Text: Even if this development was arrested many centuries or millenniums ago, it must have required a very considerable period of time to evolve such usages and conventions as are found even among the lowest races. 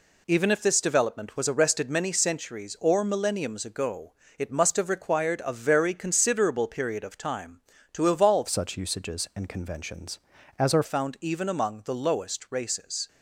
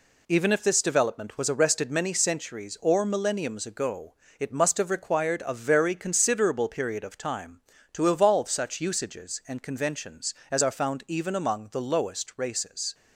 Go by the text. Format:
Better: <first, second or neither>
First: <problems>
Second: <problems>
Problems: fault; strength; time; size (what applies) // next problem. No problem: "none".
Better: second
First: changes voice from "such" to "are"; from 8.4 to 10.8 s; 2.4 s long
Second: none